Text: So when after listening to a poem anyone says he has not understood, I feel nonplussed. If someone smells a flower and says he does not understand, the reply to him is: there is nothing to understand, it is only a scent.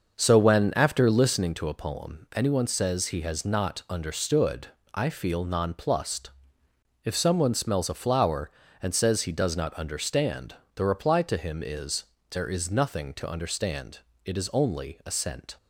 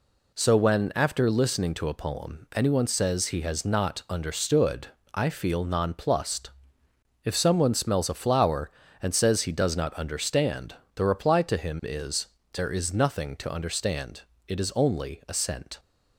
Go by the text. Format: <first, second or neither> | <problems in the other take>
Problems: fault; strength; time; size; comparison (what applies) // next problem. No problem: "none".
second | starts louder than the rest; noticeable; until 1.5 s; 6 dB